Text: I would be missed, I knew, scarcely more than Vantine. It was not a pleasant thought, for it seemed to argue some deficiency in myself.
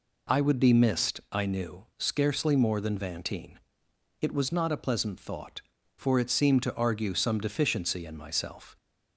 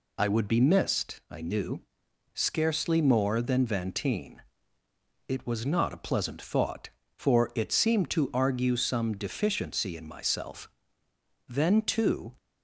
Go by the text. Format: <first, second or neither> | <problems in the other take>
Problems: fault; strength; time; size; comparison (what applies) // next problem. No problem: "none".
first | goes on to say "Then too"; noticeable; from 11.4 s on; 0.86 s long